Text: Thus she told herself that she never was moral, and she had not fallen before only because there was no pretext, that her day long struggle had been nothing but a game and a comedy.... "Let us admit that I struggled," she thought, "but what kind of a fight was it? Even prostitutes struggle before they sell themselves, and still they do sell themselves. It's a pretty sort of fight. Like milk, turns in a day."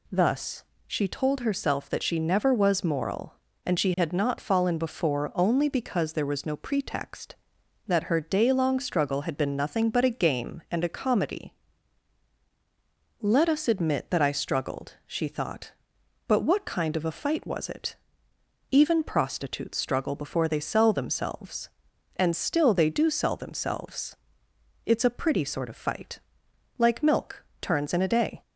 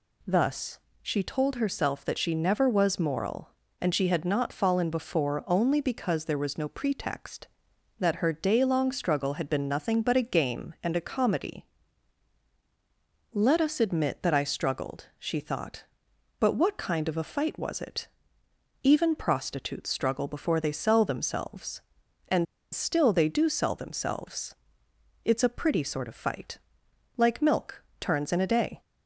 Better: first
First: pauses between "Thus" and "she"; slight; at 0.6 s; 0.24 s long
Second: pauses between "Thus" and "she"; slight; at 0.7 s; 0.24 s long // pauses between "and" and "still"; slight; at 22.4 s; 0.29 s long

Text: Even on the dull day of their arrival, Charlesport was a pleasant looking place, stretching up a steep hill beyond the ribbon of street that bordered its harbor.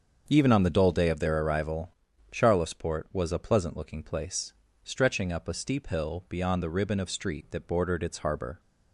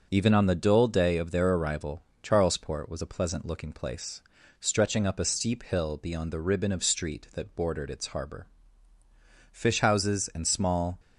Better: first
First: starts louder than the rest; until 1.2 s; 6.5 dB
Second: starts louder than the rest; until 1.1 s; 6 dB // goes on to say "Fish houses and small"; from 9.5 s on; 1.4 s long

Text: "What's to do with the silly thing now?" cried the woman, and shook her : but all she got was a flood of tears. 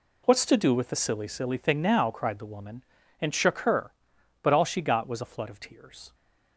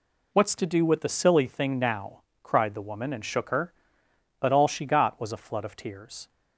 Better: second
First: says "silly" twice; at 1.2 s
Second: none

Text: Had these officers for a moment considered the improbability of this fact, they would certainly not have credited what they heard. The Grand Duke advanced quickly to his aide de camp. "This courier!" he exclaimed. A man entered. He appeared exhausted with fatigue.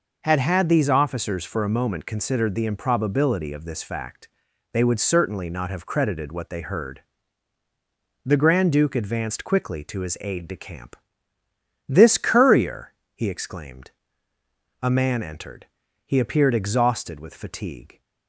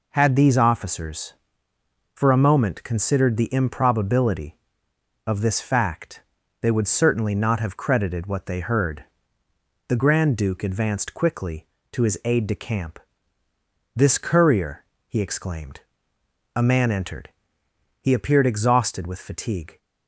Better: second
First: says "Had" twice; at 0.3 s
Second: none

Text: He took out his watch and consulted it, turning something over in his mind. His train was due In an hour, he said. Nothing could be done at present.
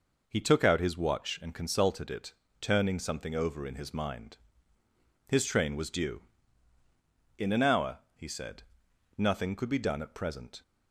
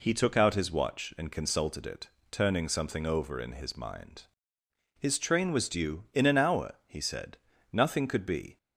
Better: first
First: none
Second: stops before "done at present"; at 8.5 s

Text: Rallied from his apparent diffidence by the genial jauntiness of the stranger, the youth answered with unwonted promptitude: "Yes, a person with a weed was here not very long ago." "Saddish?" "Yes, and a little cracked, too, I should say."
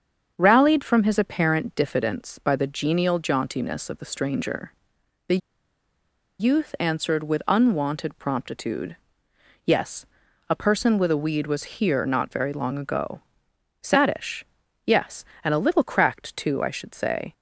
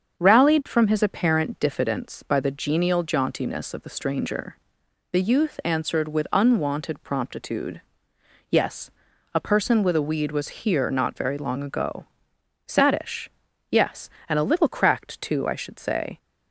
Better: second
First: starts louder than the rest; until 1.3 s; 7 dB // pauses between "the" and "youth"; at 5.3 s; 1.0 s long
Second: starts louder than the rest; until 1.2 s; 7 dB

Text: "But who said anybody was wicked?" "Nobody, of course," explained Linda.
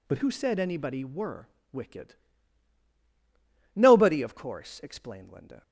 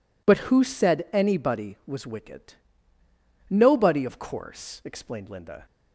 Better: second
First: says "were" for "was"; at 1.0 s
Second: none

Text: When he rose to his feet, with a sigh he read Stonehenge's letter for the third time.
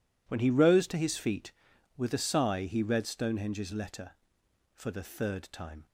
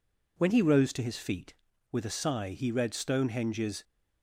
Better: first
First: none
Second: stops before "letter for the third time"; at 3.8 s

